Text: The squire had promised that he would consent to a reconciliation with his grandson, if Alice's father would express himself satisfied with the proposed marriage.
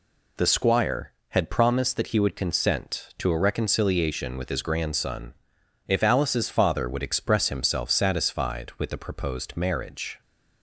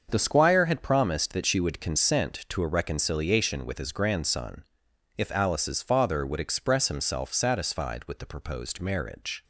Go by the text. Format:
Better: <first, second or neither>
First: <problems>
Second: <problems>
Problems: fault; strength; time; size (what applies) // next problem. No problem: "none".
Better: first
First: none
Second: starts louder than the rest; until 1.1 s; 6.5 dB // says "she" for "he"; at 1.4 s